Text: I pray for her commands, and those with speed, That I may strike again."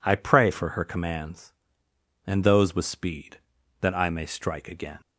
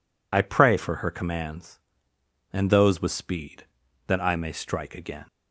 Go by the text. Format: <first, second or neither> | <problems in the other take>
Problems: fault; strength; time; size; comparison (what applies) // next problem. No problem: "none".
first | loses the start of "I"; at 0.3 s; 40 ms